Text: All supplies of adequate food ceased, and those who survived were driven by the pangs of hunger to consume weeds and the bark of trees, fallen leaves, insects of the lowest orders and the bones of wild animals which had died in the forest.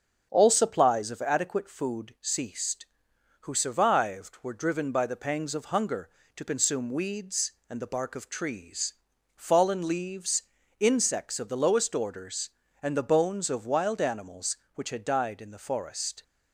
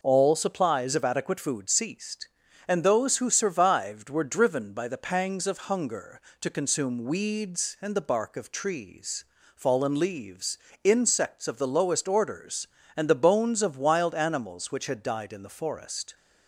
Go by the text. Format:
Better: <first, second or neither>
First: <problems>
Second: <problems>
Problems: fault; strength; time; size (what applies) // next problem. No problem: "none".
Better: second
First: starts louder than the rest; until 1.3 s; 6.5 dB // skips "and those"; at 3.1 s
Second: none